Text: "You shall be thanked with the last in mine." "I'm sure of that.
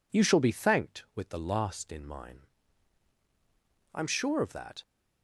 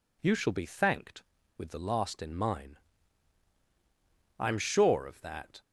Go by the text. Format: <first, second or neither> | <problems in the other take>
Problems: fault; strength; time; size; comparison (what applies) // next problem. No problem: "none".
neither | none